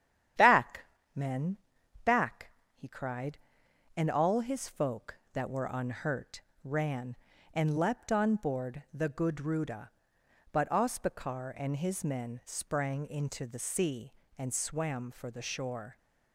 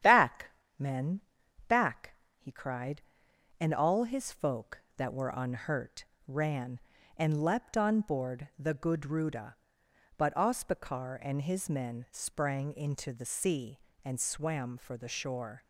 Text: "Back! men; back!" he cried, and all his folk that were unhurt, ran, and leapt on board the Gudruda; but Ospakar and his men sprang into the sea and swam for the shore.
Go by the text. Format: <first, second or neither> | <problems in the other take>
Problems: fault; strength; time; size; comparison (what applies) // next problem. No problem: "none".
neither | starts louder than the rest; strong; the same in both